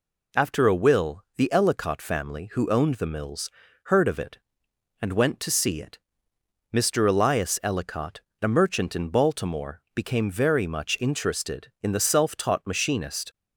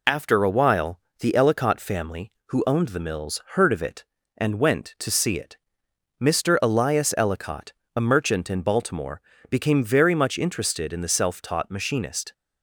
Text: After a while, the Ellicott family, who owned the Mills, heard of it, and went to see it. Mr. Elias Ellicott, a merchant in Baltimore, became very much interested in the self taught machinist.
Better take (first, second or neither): second